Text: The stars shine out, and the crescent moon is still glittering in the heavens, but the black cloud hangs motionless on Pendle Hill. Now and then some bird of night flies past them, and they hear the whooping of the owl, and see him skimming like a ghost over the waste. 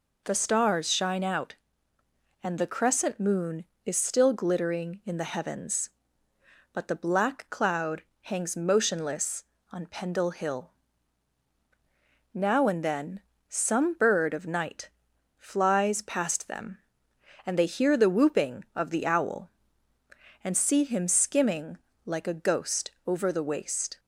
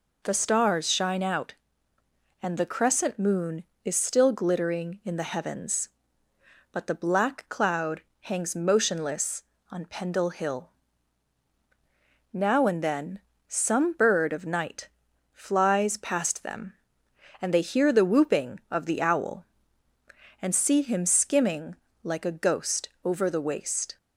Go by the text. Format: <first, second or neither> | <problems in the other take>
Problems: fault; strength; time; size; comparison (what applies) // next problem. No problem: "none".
neither | pauses between "cloud" and "hangs"; slight; the same in both // pauses between "then" and "some"; slight; the same in both // pauses between "night" and "flies"; the same in both // pauses between "skimming" and "like"; slight; the same in both // pauses between "ghost" and "over"; slight; the same in both